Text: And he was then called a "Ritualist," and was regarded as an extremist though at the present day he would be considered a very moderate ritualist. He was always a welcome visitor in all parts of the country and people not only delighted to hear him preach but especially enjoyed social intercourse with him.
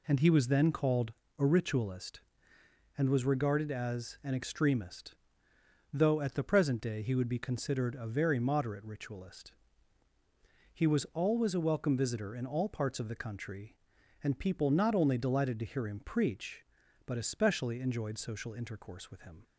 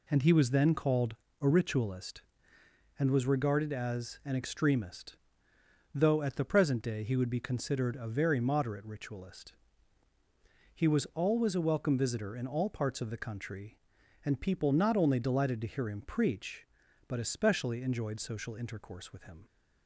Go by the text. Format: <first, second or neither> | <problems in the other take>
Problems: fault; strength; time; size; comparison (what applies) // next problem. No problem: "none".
neither | pauses between "called" and "a"; slight; the same in both // pauses between "extremist" and "though"; noticeable; the same in both